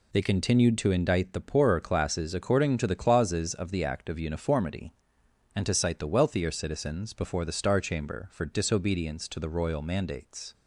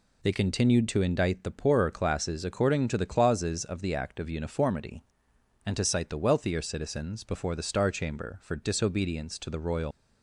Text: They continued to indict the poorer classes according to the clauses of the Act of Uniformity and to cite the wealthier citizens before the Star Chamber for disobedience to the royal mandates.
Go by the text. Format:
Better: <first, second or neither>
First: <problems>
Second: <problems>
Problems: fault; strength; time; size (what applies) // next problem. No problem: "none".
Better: first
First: none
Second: stops before "mandates"; at 9.9 s